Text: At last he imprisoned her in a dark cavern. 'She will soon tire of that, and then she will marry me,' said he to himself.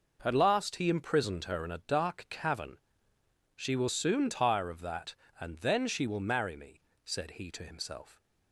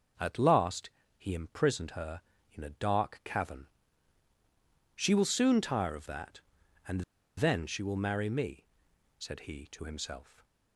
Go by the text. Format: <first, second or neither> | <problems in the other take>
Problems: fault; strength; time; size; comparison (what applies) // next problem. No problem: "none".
first | pauses between "last" and "he"; slight; at 0.9 s; 0.28 s long // pauses between "and" and "then"; slight; at 7.0 s; 0.35 s long